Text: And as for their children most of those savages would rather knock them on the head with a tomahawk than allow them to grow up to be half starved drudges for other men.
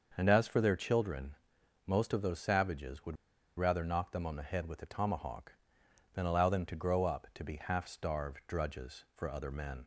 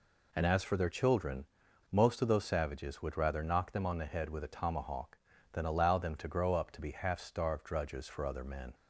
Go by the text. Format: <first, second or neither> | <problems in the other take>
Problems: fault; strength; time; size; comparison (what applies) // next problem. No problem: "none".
second | starts louder than the rest; until 1.1 s; 6.5 dB // pauses between "children" and "most"; noticeable; at 1.3 s; 0.50 s long; noticeable in the second // pauses between "would" and "rather"; at 3.1 s; 0.41 s long